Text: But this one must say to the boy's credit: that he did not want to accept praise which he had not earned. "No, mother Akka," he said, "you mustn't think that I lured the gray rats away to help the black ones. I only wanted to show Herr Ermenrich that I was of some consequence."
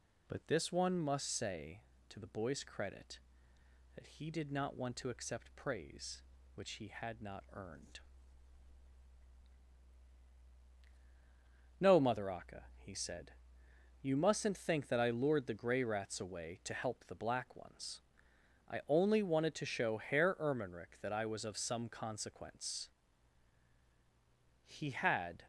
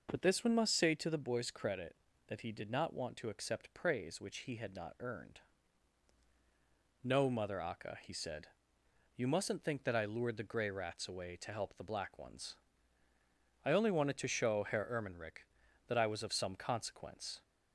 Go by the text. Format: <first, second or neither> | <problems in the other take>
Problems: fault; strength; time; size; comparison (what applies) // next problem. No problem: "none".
second | goes on to say "He had"; noticeable; from 24.6 s on; 0.82 s long